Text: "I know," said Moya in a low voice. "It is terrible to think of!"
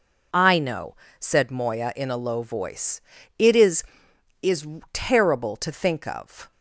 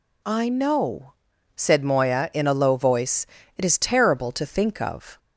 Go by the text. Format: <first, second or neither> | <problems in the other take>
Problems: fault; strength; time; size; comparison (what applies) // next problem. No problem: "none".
second | says "is" twice; at 4.4 s